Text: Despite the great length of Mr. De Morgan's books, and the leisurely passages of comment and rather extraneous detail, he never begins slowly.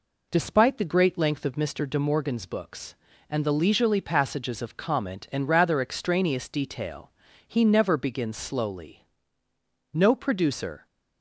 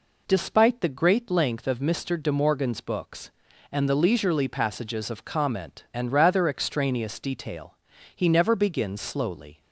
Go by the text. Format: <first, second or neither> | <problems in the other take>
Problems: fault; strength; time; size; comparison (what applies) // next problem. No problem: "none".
second | goes on to say "No producer"; noticeable; from 9.9 s on; 0.92 s long